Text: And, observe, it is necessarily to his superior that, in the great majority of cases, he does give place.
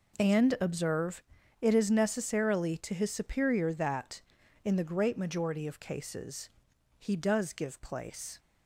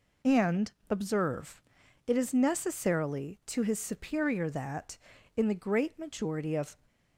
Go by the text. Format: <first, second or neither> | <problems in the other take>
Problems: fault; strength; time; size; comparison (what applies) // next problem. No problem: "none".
first | stops before "cases he does give place"; at 6.8 s